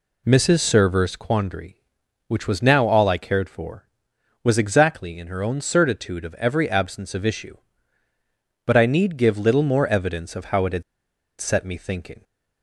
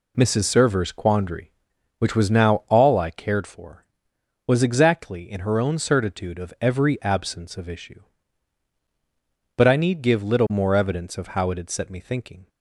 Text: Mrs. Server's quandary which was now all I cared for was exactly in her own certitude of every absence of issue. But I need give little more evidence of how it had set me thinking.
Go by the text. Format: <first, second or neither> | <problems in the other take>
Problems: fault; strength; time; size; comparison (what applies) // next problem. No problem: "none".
second | pauses between "had" and "set"; noticeable; at 10.8 s; 0.58 s long